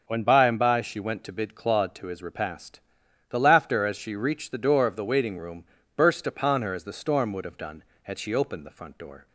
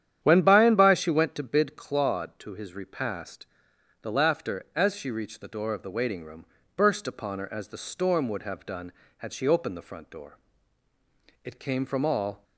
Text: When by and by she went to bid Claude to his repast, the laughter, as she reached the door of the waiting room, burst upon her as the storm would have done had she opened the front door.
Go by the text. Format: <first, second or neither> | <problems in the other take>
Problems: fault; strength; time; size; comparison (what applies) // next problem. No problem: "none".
first | starts louder than the rest; strong; until 1.2 s; 10 dB; also in the first // goes on to say "It came from all"; noticeable; from 11.4 s on; 1.0 s long